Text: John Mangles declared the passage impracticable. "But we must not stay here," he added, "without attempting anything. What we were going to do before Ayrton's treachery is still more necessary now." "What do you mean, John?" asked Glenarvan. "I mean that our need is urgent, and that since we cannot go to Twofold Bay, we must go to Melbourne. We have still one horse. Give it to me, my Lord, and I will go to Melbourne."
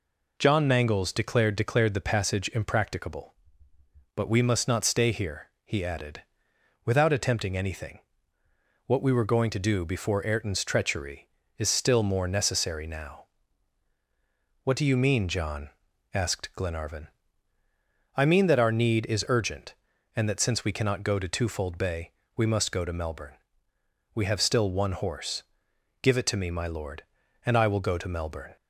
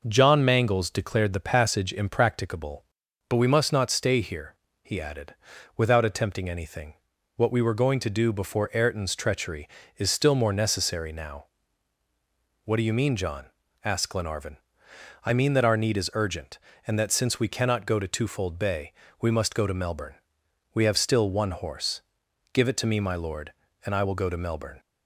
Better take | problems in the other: second | says "declared" twice; at 1.5 s

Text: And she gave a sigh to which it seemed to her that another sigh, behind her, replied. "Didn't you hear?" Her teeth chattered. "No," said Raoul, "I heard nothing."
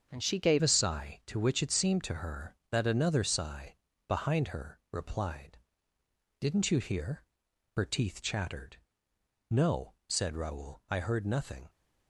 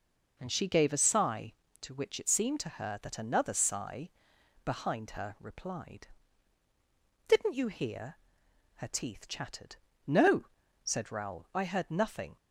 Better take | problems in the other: second | starts louder than the rest; until 1.1 s; 7 dB // changes voice at "a"; from 0.6 s on; 11.0 s long

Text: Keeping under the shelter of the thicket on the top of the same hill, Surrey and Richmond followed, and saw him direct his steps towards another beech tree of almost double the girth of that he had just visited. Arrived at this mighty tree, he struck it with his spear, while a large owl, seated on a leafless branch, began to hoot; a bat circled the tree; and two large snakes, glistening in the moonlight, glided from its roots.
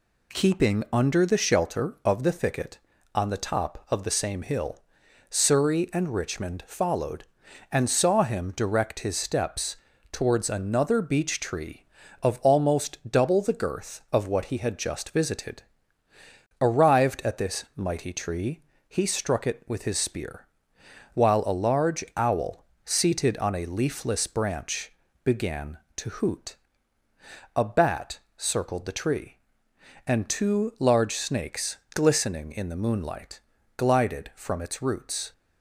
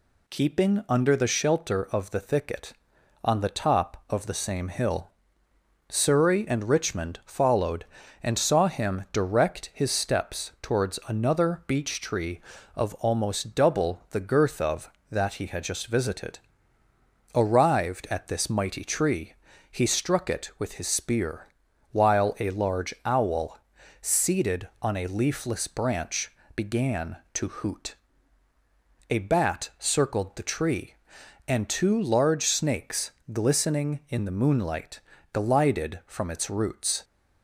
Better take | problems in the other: second | pauses between "steps" and "towards"; slight; at 9.7 s; 0.36 s long // says "what" for "that"; at 14.2 s // pauses between "bat" and "circled"; slight; at 28.1 s; 0.18 s long

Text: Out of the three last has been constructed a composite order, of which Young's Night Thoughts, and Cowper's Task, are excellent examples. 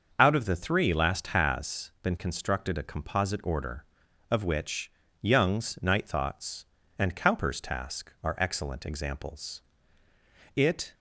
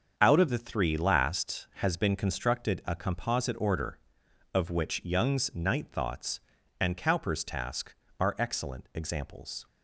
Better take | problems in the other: second | starts louder than the rest; until 1.1 s; 6.5 dB; also in the second // pauses between "which" and "Young's"; slight; at 4.9 s; 0.30 s long // goes on to say "It"; slight; from 10.5 s on; 0.38 s long

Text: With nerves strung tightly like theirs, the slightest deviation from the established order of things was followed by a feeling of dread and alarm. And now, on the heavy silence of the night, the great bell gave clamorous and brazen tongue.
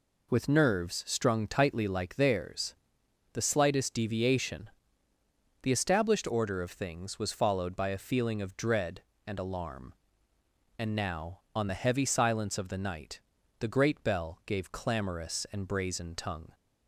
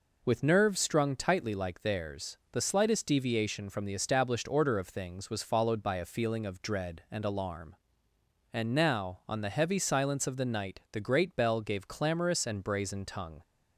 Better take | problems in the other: second | skips "from"; at 5.1 s

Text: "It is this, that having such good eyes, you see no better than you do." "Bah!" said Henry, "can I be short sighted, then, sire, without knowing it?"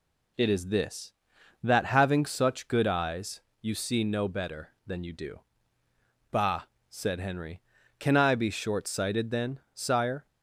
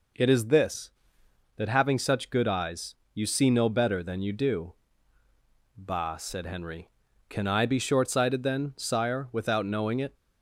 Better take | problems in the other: second | stops before "without knowing it"; at 10.2 s

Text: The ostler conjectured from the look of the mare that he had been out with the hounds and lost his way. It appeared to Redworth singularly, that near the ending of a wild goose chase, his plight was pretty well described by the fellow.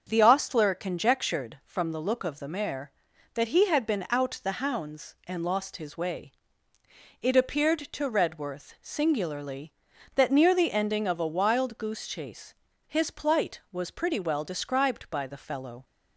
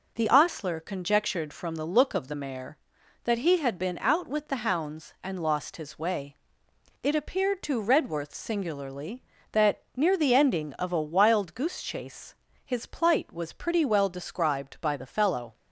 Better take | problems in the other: second | starts louder than the rest; until 1.0 s; 6.5 dB // skips "with"; at 4.4 s

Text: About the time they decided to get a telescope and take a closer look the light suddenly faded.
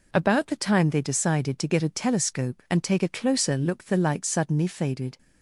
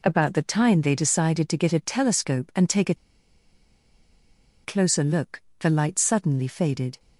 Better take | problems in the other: first | pauses between "a" and "closer"; strong; at 2.9 s; 1.7 s long // pauses between "look" and "the"; slight; at 5.4 s; 0.20 s long

